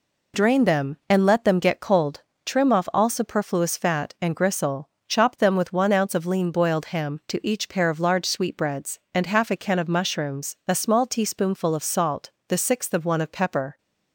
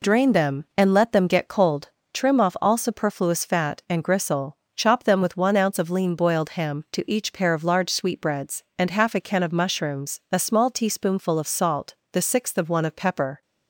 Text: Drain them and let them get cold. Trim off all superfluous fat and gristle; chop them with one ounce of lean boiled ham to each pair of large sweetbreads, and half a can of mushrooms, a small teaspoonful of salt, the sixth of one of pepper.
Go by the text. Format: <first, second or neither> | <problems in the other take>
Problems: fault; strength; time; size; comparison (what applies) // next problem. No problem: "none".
neither | none